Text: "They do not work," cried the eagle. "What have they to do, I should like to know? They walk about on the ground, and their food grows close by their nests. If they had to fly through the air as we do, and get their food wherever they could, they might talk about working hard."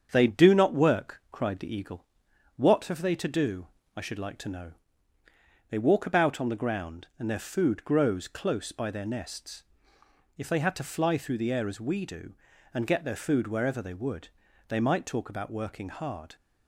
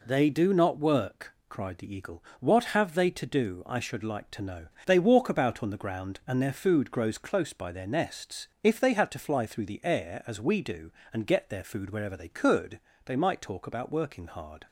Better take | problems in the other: second | starts louder than the rest; strong; until 1.1 s; 7.5 dB // says "would" for "could"; at 13.9 s

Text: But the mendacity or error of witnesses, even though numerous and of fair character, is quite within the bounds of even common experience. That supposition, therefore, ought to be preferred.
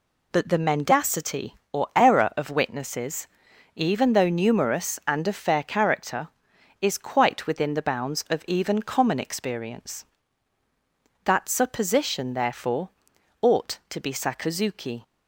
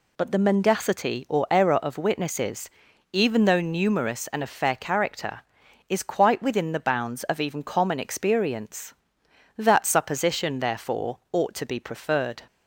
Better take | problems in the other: second | says "sakazuki" for "preferred"; at 14.1 s

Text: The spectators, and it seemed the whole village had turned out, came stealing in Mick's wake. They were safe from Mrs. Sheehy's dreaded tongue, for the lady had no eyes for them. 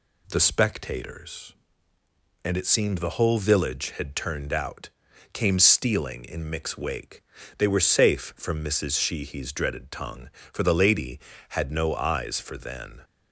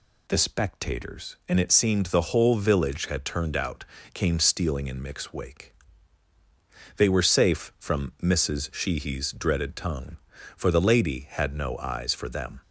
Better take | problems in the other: second | says "then" for "them"; at 12.5 s

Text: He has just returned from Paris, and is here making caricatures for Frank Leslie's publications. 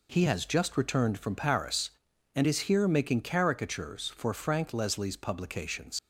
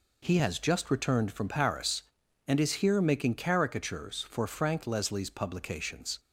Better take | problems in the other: second | leaves "publications" unfinished; at 5.9 s; 75 ms

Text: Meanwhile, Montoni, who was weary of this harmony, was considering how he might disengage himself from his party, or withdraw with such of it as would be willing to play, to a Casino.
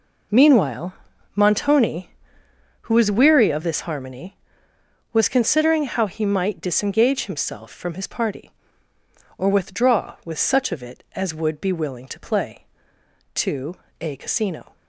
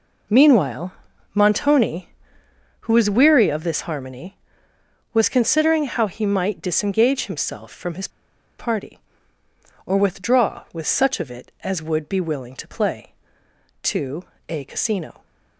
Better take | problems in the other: first | pauses between "his" and "party"; noticeable; at 8.0 s; 0.50 s long // pauses between "to" and "a"; slight; at 14.2 s; 0.26 s long; slight in the first

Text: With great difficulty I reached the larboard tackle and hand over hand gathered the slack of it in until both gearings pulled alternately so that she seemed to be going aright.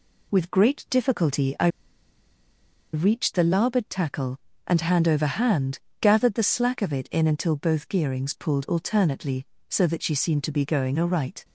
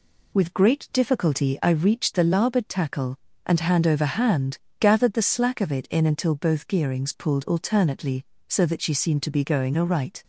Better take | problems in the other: second | pauses between "I" and "reached"; strong; at 1.6 s; 1.2 s long // pauses between "hand" and "gathered"; slight; at 5.8 s; 0.20 s long; slight in the second

